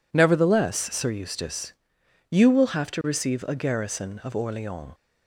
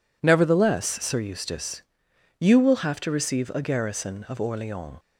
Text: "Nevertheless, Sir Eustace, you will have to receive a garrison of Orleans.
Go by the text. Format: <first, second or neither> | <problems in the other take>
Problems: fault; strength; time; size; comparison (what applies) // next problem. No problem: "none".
neither | none